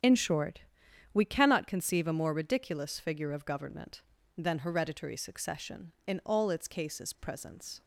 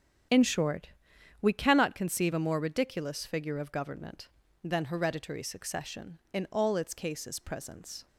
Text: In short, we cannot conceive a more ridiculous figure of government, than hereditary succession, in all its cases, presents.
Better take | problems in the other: neither | starts louder than the rest; strong; the same in both

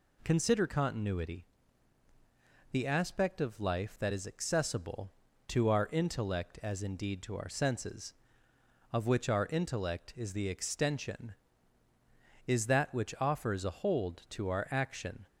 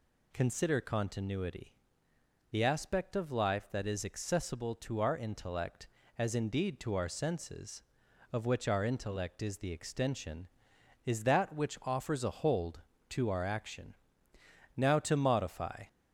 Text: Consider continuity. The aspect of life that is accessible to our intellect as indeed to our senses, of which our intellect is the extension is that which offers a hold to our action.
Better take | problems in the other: first | goes on to say "Now to modify"; noticeable; from 14.7 s on; 1.1 s long

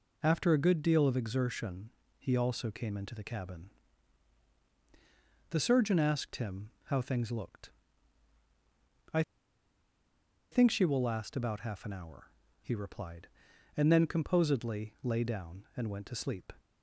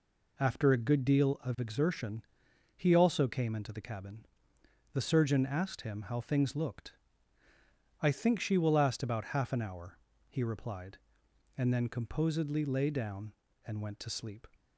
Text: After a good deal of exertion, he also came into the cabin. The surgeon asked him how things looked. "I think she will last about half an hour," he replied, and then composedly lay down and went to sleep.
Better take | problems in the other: second | pauses between "I" and "think"; strong; at 9.2 s; 1.3 s long

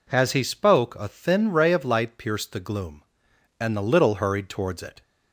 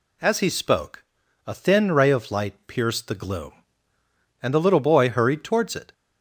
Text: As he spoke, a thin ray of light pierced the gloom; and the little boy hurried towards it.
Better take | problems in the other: second | skips "boy"; at 4.1 s

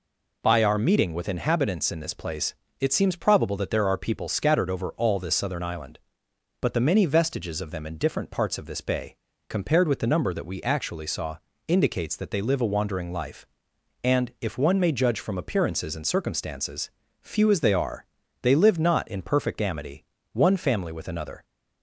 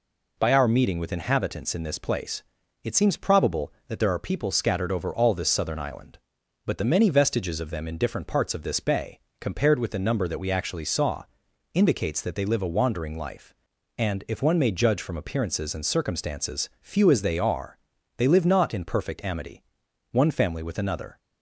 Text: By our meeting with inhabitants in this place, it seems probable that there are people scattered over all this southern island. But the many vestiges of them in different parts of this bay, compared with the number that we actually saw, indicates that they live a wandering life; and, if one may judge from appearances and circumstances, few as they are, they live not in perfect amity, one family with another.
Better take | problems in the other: neither | none

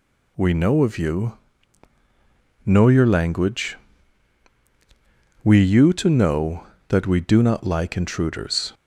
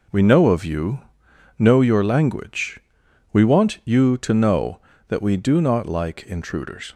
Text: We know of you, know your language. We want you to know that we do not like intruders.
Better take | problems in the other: second | skips "want"; at 5.6 s

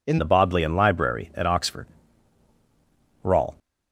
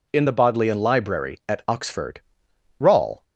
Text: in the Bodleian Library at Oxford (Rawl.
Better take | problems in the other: second | changes voice at "the"; from 0.1 s on; 3.4 s long

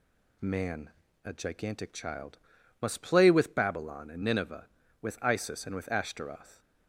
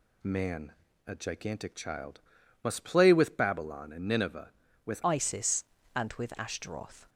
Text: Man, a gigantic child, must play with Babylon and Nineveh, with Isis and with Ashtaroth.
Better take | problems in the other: first | changes voice at "Isis"; from 5.0 s on; 2.0 s long

